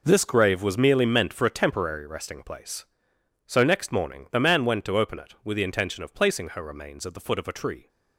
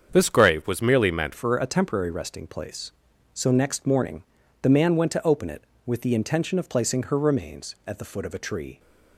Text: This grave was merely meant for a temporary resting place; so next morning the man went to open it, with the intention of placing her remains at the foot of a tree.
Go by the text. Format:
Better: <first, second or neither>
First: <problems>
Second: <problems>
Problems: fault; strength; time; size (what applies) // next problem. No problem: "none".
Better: first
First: none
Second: starts louder than the rest; strong; until 1.1 s; 7.5 dB // changes voice at "for"; from 1.3 s on; 7.4 s long // pauses between "morning" and "the"; at 4.2 s; 0.40 s long